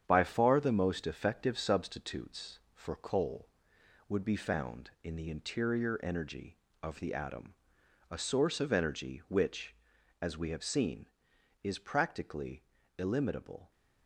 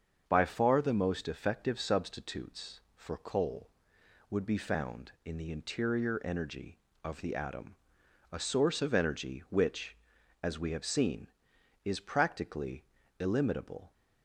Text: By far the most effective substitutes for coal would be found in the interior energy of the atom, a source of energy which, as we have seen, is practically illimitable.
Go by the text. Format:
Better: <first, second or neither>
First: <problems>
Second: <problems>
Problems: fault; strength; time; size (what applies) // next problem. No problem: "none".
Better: second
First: gets quieter; noticeable; throughout; 5 dB // starts louder than the rest; strong; until 1.0 s; 8.5 dB // pauses between "practically" and "illimitable"; slight; at 12.6 s; 0.36 s long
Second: starts louder than the rest; until 1.2 s; 7 dB // pauses between "practically" and "illimitable"; slight; at 12.8 s; 0.36 s long